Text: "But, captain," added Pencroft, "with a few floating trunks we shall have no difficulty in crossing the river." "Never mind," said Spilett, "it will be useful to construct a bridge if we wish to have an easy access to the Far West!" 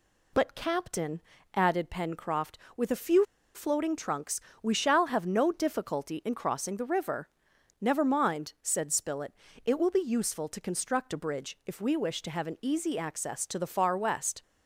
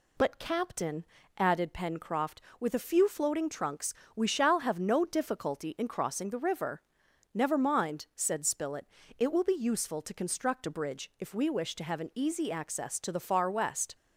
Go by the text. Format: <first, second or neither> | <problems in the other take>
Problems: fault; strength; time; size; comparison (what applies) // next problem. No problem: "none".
second | pauses between "few" and "floating"; slight; at 3.2 s; 0.30 s long // pauses between "trunks" and "we"; slight; at 4.3 s; 0.22 s long; slight in the second